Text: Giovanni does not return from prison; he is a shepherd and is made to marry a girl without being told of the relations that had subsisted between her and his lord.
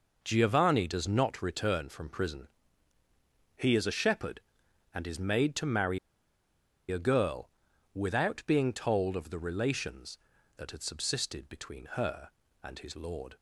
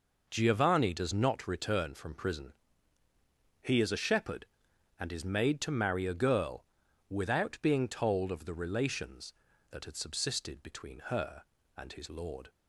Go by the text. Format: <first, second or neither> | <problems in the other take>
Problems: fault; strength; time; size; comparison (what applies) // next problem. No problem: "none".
second | pauses between "marry" and "a"; noticeable; at 5.9 s; 0.92 s long // pauses between "girl" and "without"; noticeable; at 7.4 s; 0.46 s long; noticeable in the second